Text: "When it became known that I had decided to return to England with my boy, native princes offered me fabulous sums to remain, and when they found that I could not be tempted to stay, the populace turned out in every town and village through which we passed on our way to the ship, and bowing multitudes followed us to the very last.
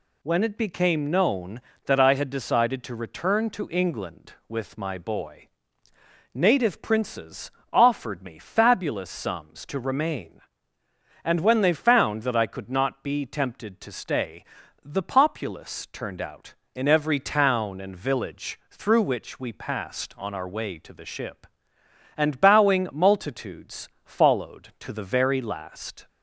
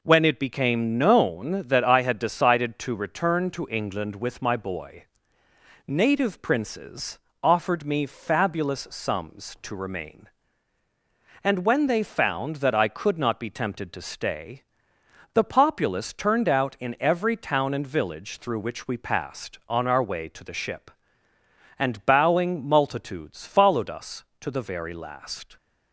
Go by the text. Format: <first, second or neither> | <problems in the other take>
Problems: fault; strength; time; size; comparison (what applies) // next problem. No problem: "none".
second | pauses between "princes" and "offered"; slight; at 7.5 s; 0.20 s long; slight in the second // pauses between "multitudes" and "followed"; slight; at 23.8 s; 0.16 s long // skips "us"; at 24.7 s